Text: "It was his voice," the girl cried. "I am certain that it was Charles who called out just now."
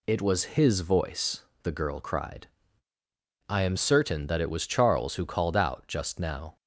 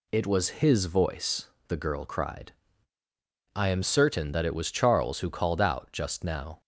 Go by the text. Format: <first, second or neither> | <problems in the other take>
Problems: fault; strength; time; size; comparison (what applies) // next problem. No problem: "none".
neither | none